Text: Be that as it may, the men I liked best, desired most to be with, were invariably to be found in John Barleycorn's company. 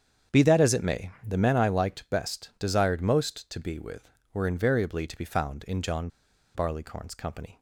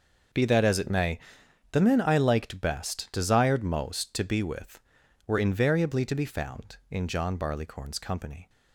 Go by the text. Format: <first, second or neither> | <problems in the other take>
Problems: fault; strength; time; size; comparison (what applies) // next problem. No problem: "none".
second | starts louder than the rest; strong; until 1.4 s; 8 dB; noticeable in the second // pauses between "John" and "Barleycorn's"; noticeable; at 6.0 s; 0.47 s long